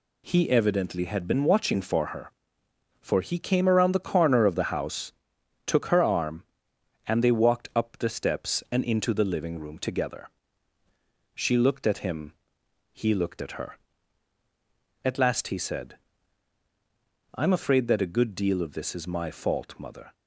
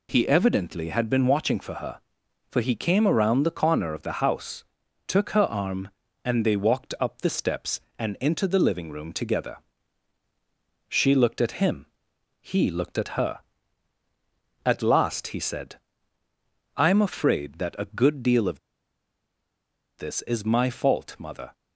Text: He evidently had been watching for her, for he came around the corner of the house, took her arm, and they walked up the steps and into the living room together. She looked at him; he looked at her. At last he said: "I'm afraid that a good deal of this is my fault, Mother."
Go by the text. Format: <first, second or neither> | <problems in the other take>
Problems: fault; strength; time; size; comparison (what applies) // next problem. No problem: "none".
first | pauses between "of" and "this"; strong; at 18.5 s; 1.4 s long